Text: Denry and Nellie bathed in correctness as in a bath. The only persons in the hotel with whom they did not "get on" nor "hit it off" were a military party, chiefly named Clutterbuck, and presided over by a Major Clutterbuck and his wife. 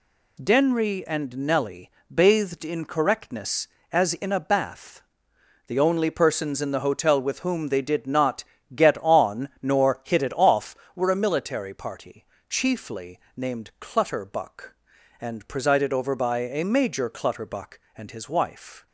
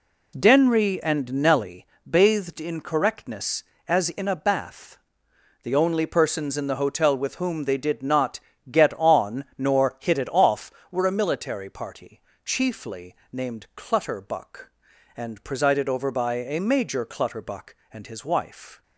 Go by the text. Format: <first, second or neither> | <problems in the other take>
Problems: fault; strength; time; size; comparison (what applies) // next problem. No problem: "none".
first | starts louder than the rest; slight; until 1.8 s; 2 dB // pauses between "Nellie" and "bathed"; slight; at 1.8 s; 0.22 s long; slight in the first // pauses between "not" and "get"; slight; at 8.4 s; 0.28 s long; slight in the first // pauses between "chiefly" and "named"; slight; at 13.1 s; 0.16 s long; slight in the first